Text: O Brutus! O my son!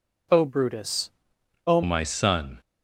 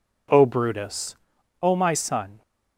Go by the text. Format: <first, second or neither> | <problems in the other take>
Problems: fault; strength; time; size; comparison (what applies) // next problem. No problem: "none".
second | changes voice at "my"; from 1.8 s on; 0.7 s long